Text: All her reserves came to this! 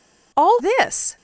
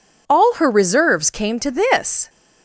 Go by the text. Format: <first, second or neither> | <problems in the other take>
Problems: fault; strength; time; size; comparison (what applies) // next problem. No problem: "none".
second | skips "her reserves came to"; at 0.5 s